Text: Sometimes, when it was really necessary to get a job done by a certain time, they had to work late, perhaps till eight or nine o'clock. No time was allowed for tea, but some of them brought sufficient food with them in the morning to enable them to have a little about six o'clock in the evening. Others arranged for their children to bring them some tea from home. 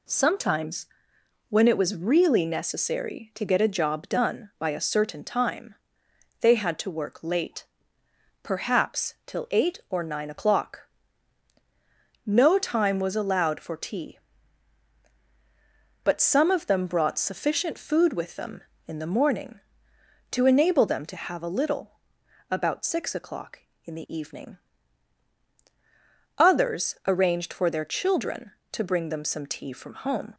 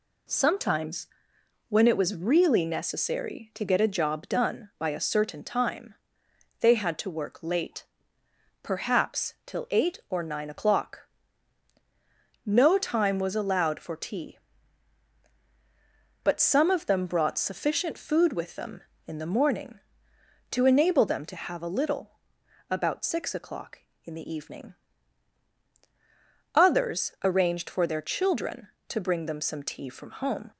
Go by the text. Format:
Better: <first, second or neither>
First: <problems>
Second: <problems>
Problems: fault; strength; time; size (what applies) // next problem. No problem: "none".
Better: neither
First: pauses between "little" and "about"; noticeable; at 21.9 s; 0.58 s long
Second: pauses between "little" and "about"; noticeable; at 22.1 s; 0.58 s long